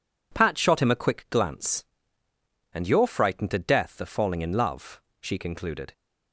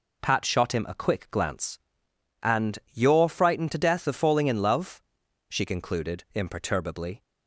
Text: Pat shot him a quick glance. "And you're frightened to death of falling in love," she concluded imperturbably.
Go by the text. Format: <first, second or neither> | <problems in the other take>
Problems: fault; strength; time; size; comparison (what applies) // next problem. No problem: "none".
second | stops before "imperturbably"; at 5.9 s